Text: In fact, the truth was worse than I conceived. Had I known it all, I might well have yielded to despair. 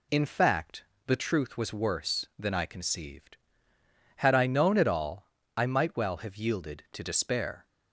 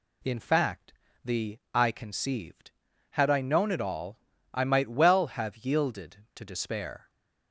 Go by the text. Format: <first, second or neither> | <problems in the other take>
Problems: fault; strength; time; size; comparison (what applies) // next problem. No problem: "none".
first | skips "truth was worse than"; at 1.6 s